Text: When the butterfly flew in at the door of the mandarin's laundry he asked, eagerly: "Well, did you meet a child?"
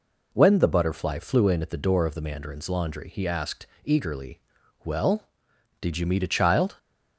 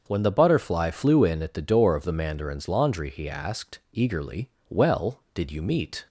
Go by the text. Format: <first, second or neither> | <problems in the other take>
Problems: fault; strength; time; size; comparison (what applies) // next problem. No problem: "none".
first | starts louder than the rest; until 1.0 s; 6.5 dB // stops before "a child"; at 6.0 s